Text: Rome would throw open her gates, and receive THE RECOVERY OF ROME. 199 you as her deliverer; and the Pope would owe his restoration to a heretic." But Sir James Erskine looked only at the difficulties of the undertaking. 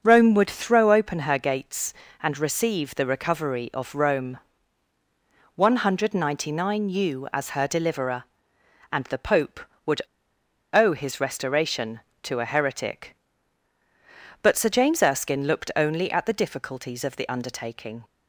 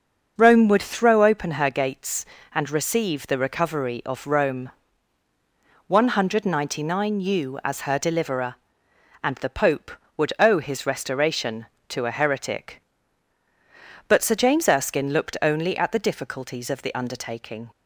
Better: second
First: starts louder than the rest; until 1.0 s; 6.5 dB // pauses between "would" and "owe"; noticeable; at 10.0 s; 0.71 s long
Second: starts louder than the rest; until 1.3 s; 6.5 dB

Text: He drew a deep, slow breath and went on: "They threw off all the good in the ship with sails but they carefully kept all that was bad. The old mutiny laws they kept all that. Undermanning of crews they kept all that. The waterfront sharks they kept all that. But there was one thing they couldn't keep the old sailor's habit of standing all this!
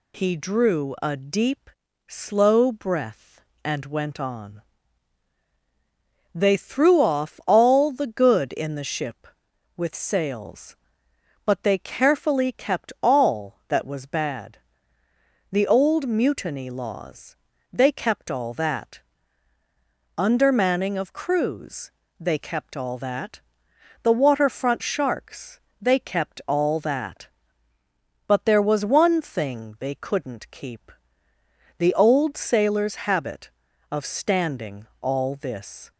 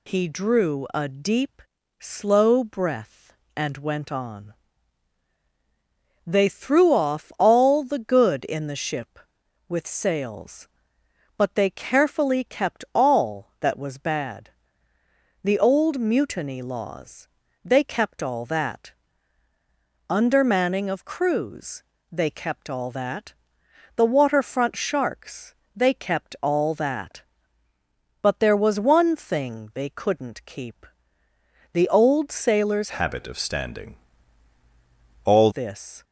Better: first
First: pauses between "laws" and "they"; at 17.3 s; 0.38 s long // pauses between "crews" and "they"; slight; at 21.9 s; 0.30 s long // pauses between "sharks" and "they"; slight; at 25.5 s; 0.22 s long // pauses between "keep" and "the"; noticeable; at 30.9 s; 0.86 s long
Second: pauses between "laws" and "they"; at 17.2 s; 0.38 s long // pauses between "crews" and "they"; slight; at 21.8 s; 0.30 s long // pauses between "sharks" and "they"; slight; at 25.5 s; 0.22 s long // pauses between "keep" and "the"; noticeable; at 30.8 s; 0.86 s long // changes voice from "habit" to "all"; from 32.8 to 35.5 s; 2.7 s long // pauses between "standing" and "all"; strong; at 33.9 s; 1.3 s long

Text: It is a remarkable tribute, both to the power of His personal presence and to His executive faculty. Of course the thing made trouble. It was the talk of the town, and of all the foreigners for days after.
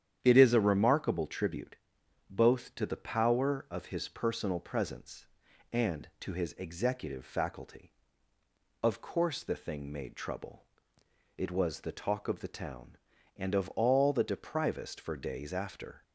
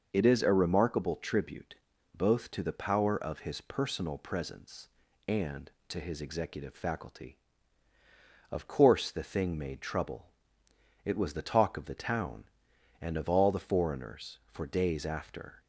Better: second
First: starts louder than the rest; strong; until 1.2 s; 9.5 dB // says "deprivest" for "foreigners"; at 14.2 s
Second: none

